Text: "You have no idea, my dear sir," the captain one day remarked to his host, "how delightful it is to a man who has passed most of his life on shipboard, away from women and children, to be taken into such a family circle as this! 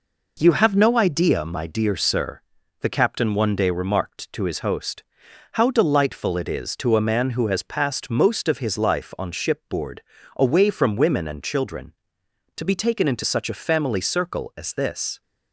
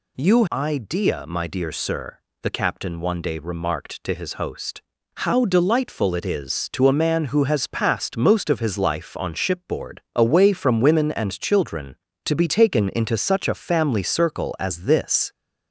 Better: first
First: none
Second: skips "have no"; at 0.4 s

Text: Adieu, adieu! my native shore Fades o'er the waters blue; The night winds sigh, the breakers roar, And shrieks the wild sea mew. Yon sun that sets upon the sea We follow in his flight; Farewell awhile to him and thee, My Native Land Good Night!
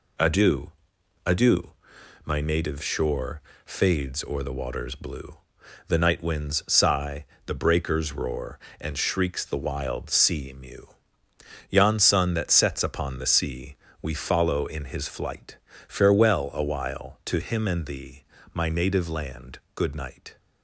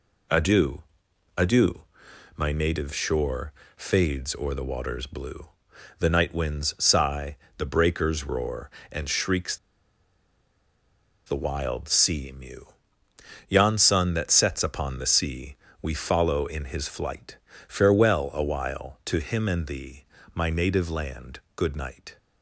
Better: first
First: pauses between "shore" and "Fades"; slight; at 3.4 s; 0.24 s long // pauses between "sea" and "We"; slight; at 13.7 s; 0.26 s long // pauses between "Land" and "Good"; slight; at 19.5 s; 0.16 s long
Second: pauses between "shore" and "Fades"; slight; at 3.5 s; 0.24 s long // pauses between "shrieks" and "the"; strong; at 9.5 s; 1.7 s long // pauses between "sea" and "We"; slight; at 15.5 s; 0.26 s long // pauses between "Land" and "Good"; slight; at 21.3 s; 0.16 s long

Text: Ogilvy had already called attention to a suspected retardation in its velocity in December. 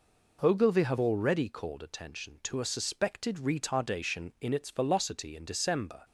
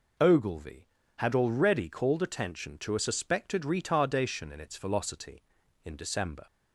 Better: second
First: says "have" for "had"; at 0.8 s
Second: none

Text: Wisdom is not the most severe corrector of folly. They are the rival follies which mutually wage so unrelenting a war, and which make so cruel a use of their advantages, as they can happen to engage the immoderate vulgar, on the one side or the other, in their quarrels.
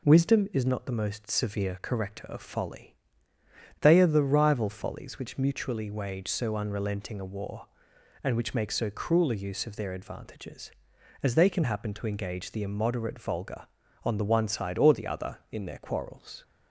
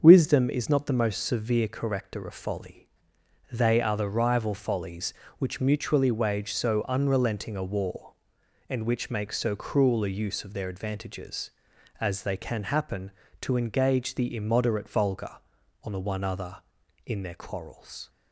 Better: first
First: none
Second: starts louder than the rest; until 1.0 s; 6 dB // skips "side or the"; at 16.2 s

